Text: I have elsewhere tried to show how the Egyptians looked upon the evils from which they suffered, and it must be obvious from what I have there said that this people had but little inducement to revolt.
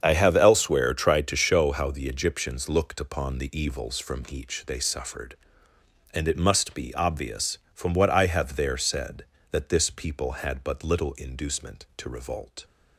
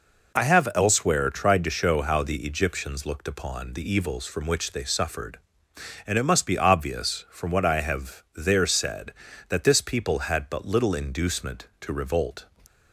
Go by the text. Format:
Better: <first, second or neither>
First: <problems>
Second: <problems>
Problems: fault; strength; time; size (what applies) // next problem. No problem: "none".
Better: second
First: starts louder than the rest; strong; until 1.0 s; 7.5 dB // says "each" for "which"; at 4.3 s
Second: none